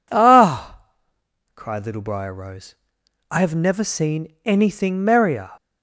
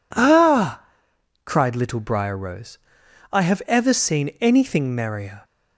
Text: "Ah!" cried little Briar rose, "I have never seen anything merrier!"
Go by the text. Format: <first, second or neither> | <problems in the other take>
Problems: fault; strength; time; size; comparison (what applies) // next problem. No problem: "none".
first | says "ever" for "never"; at 3.6 s